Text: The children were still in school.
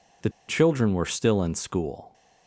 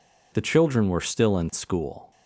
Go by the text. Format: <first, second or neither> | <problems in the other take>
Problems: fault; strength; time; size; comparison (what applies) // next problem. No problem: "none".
second | pauses between "The" and "children"; slight; at 0.2 s; 0.19 s long